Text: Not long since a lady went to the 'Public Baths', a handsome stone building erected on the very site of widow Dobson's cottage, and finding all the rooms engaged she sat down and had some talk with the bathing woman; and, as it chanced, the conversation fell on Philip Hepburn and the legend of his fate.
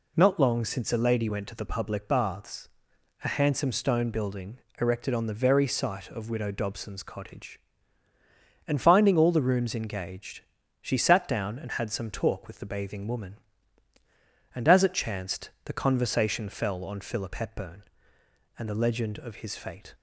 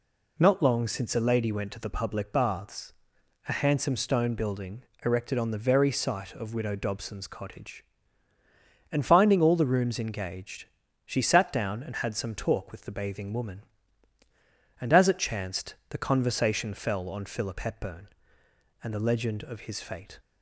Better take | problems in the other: neither | pauses between "building" and "erected"; slight; the same in both // pauses between "engaged" and "she"; the same in both

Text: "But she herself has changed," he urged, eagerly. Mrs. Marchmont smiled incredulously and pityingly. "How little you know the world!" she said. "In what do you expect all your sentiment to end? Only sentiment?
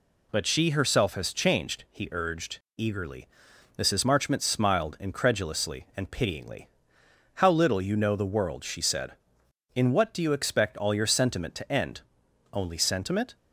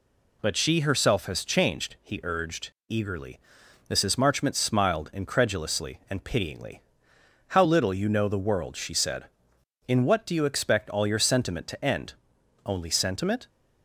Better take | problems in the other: neither | none

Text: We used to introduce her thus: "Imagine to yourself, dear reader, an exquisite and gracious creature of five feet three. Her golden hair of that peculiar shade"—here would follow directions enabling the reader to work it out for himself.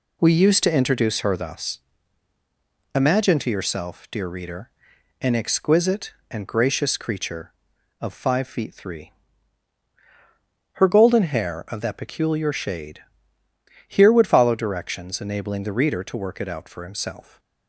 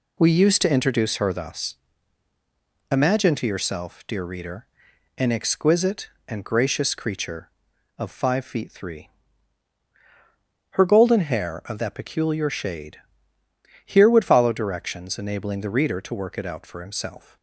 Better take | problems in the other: neither | none

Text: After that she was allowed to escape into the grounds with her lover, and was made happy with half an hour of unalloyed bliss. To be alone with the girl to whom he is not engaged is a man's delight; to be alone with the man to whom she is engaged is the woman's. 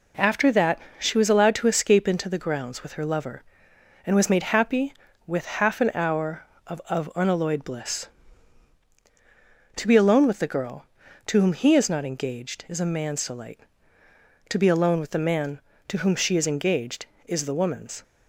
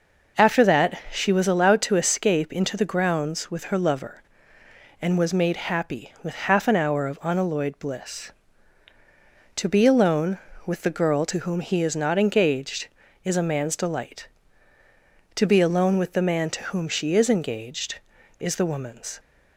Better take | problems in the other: second | pauses between "that" and "she"; slight; at 0.7 s; 0.18 s long // says "of" twice; at 6.8 s

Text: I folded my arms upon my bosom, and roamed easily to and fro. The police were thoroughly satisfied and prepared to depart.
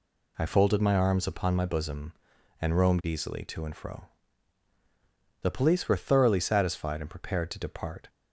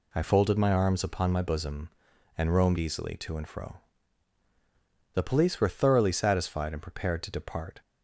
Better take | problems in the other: neither | none

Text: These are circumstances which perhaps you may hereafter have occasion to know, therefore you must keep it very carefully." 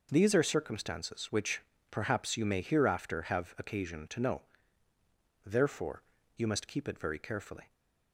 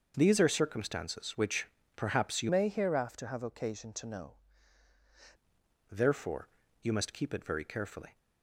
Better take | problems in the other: first | starts louder than the rest; noticeable; until 1.1 s; 6 dB // pauses between "which" and "perhaps"; slight; at 1.6 s; 0.32 s long; slight in the first // changes voice from "may" to "know"; from 2.4 to 4.3 s; 1.9 s long // pauses between "therefore" and "you"; slight; at 6.4 s; 0.34 s long; slight in the first

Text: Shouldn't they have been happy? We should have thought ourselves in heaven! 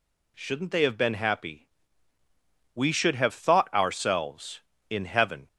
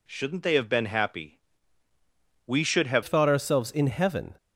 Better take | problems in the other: first | changes voice at "thought"; from 3.0 s on; 1.3 s long

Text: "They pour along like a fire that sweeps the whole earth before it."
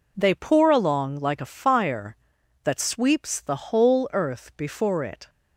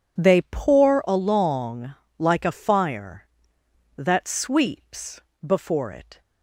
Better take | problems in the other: first | pauses between "along" and "like"; slight; at 1.9 s; 0.24 s long // skips "the whole earth"; at 5.3 s

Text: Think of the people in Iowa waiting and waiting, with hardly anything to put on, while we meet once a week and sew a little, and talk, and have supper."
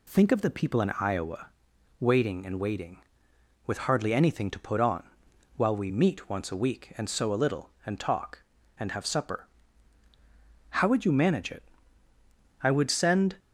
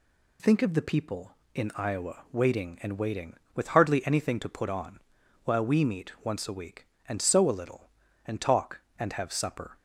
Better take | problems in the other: second | pauses between "Iowa" and "waiting"; noticeable; at 1.4 s; 0.50 s long // goes on to say "How would you manage it I would send"; strong; from 10.7 s on; 2.6 s long

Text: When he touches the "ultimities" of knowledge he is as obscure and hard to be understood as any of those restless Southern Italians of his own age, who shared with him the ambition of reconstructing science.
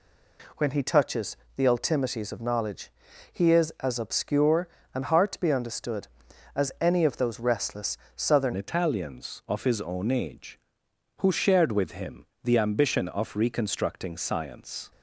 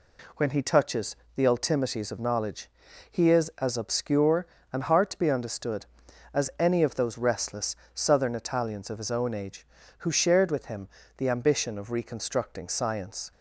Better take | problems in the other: second | pauses between "touches" and "the"; slight; at 1.3 s; 0.20 s long; slight in the second // pauses between "knowledge" and "he"; at 2.9 s; 0.40 s long; also in the second // pauses between "restless" and "Southern"; slight; at 7.9 s; 0.18 s long; slight in the second // changes voice at "Italians"; from 8.5 s on; 6.4 s long // pauses between "him" and "the"; slight; at 12.2 s; 0.20 s long; slight in the second

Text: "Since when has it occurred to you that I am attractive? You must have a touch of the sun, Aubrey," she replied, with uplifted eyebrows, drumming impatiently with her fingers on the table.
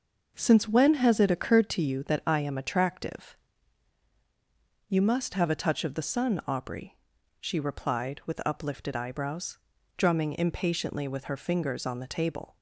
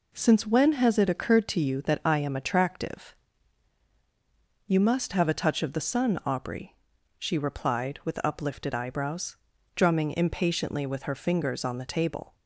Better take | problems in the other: second | starts louder than the rest; noticeable; until 1.9 s; 6 dB

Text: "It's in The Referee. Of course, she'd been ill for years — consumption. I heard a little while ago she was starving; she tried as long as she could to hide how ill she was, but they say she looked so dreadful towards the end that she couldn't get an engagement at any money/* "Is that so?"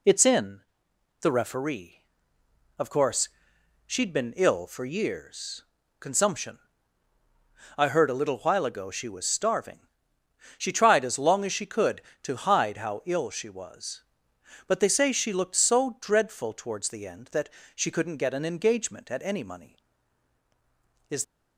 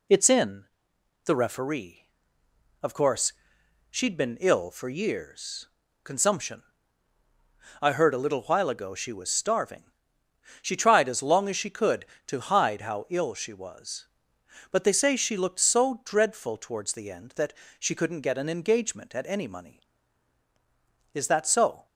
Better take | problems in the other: second | pauses between "in" and "The"; noticeable; at 0.6 s; 0.58 s long; noticeable in the second // pauses between "that" and "she"; slight; at 17.4 s; 0.26 s long; slight in the second // stops before "that so"; at 21.2 s

